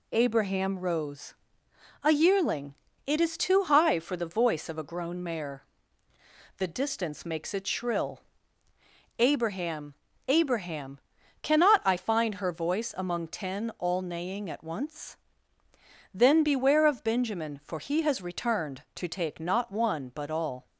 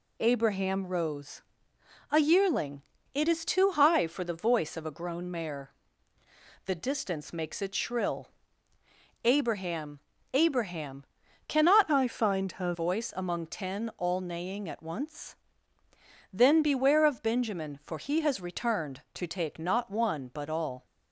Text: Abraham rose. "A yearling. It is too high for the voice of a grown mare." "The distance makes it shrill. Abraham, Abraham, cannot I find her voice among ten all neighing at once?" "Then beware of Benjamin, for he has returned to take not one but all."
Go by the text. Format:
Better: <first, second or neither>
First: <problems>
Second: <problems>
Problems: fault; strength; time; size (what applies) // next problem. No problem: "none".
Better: first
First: none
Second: changes voice from "I" to "her"; from 11.9 to 12.7 s; 0.8 s long